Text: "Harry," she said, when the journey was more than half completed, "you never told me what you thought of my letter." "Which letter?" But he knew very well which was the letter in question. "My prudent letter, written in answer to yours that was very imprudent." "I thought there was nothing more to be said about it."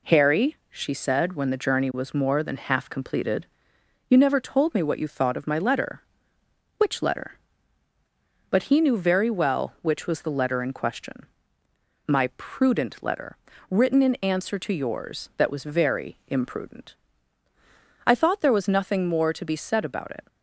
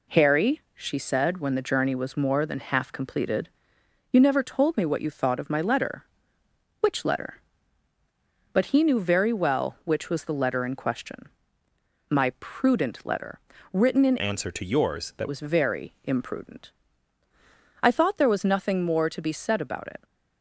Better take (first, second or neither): first